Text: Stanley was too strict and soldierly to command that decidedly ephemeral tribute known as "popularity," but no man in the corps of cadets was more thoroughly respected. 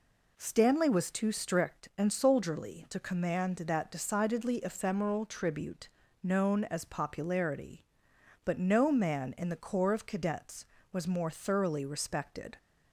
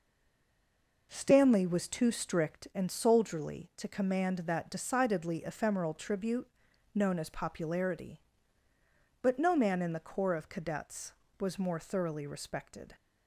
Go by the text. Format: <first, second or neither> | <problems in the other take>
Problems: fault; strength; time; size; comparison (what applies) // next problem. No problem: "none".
first | stays silent before the first word; until 1.1 s; 1.1 s long // pauses between "tribute" and "known"; noticeable; at 6.4 s; 0.48 s long; slight in the first